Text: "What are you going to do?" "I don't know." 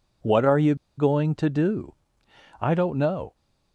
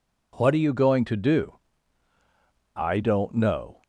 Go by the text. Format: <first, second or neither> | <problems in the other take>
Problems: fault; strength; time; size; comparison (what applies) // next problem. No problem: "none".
second | pauses between "you" and "going"; slight; at 0.7 s; 0.22 s long